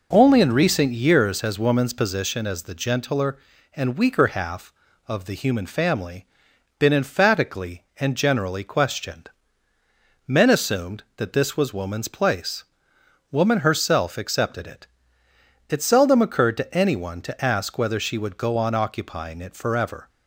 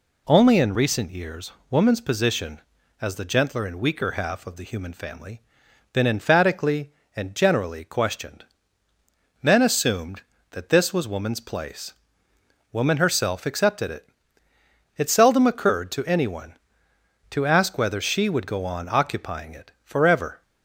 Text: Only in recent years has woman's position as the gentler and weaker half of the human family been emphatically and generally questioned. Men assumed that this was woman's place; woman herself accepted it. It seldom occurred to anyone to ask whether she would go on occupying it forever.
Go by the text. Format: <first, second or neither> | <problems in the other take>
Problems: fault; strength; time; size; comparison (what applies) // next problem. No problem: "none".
first | skips "has"; at 1.6 s // pauses between "family" and "been"; noticeable; at 5.3 s; 0.52 s long; noticeable in the first // pauses between "it" and "forever"; slight; at 19.6 s; 0.16 s long